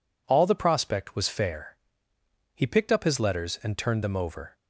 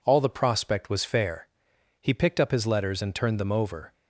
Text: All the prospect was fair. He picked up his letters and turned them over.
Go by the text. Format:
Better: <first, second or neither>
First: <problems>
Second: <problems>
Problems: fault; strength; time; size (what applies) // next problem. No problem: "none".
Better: neither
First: none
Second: none